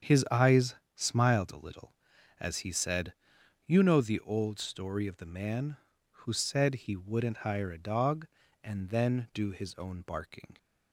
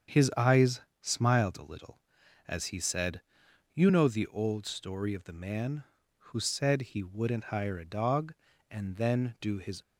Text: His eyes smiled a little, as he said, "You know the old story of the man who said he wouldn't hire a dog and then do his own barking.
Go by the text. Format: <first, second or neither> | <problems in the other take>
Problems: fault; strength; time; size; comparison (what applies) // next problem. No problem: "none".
first | starts louder than the rest; strong; until 1.3 s; 7.5 dB; strong in the first // pauses between "eyes" and "smiled"; slight; at 0.8 s; 0.22 s long; slight in the first // stops before "own barking"; at 9.8 s